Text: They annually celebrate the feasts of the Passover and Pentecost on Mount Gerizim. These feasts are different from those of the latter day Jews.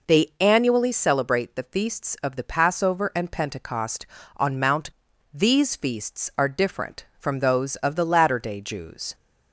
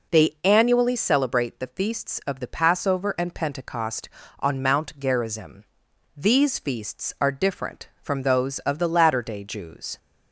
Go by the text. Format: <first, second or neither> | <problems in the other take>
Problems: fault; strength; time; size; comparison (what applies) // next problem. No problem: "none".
second | skips "Gerizim"; at 5.1 s